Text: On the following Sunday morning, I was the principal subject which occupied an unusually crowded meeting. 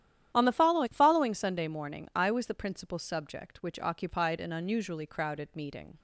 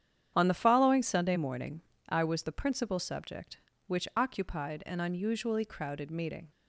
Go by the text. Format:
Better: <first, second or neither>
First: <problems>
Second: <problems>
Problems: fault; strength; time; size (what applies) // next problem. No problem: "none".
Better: second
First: starts louder than the rest; strong; until 1.3 s; 11 dB // says "following" twice; at 0.9 s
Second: starts louder than the rest; strong; until 1.3 s; 9 dB